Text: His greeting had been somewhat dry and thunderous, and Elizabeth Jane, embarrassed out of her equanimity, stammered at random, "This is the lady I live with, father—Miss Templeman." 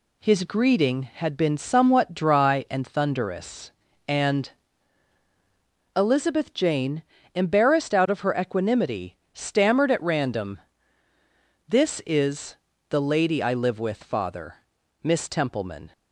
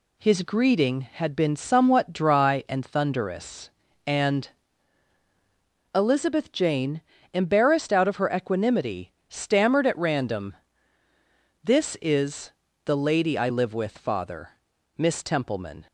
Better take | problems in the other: neither | pauses between "and" and "Elizabeth"; strong; the same in both // pauses between "is" and "the"; slight; the same in both

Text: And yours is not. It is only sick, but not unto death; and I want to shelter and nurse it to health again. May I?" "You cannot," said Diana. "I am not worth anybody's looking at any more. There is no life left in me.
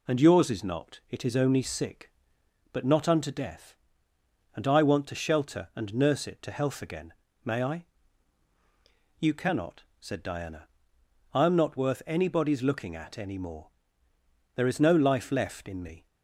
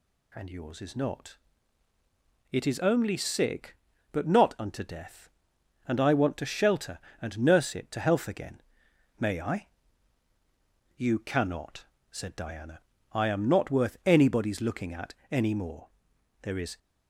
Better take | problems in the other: first | pauses between "at" and "any"; slight; at 15.1 s; 0.16 s long // stops before "no life left in me"; at 16.7 s

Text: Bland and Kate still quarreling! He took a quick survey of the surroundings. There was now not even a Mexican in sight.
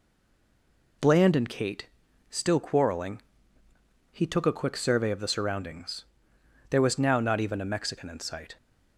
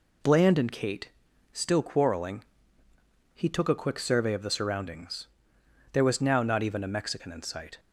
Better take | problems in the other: second | stays silent before the first word; until 1.0 s; 1.0 s long // pauses between "Kate" and "still"; at 1.8 s; 0.42 s long; also in the second

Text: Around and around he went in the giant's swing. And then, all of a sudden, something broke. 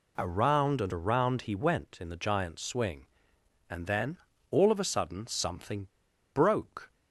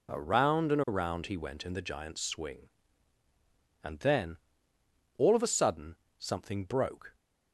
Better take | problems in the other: second | pauses between "something" and "broke"; noticeable; at 5.8 s; 0.46 s long

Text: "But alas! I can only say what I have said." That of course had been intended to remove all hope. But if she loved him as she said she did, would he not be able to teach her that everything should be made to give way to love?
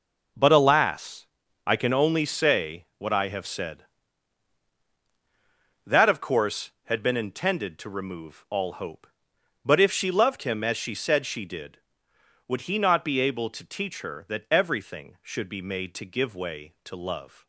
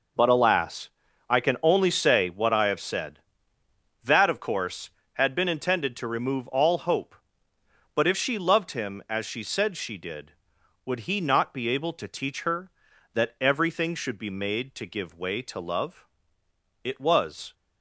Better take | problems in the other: first | goes on to say "It was"; noticeable; from 16.8 s on; 0.72 s long

